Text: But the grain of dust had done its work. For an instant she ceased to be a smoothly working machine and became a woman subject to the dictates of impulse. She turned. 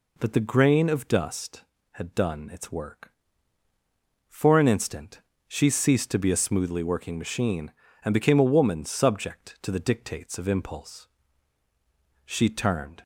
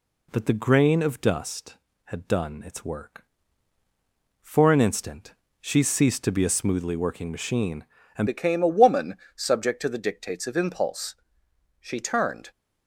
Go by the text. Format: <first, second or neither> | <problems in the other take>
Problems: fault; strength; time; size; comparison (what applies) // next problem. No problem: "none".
first | pauses between "instant" and "she"; slight; at 5.3 s; 0.28 s long; slight in the first // changes voice at "became"; from 8.2 s on; 4.3 s long // pauses between "woman" and "subject"; slight; at 9.1 s; 0.20 s long